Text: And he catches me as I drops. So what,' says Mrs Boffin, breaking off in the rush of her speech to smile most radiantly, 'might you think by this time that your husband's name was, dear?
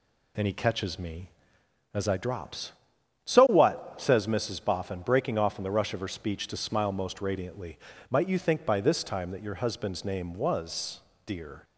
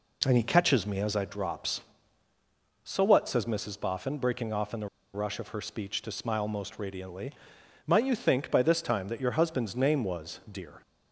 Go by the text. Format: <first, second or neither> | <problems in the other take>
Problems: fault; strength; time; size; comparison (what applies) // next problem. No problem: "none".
first | pauses between "the" and "rush"; slight; at 4.8 s; 0.27 s long